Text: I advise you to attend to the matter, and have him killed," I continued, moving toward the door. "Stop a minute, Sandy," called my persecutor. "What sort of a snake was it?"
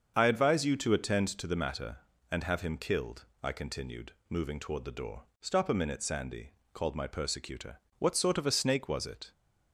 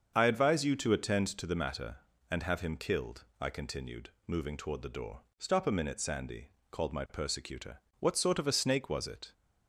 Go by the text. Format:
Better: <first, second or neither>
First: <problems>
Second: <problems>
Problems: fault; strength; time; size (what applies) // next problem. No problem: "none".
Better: neither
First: starts louder than the rest; until 1.1 s; 6.5 dB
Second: starts louder than the rest; until 1.1 s; 6.5 dB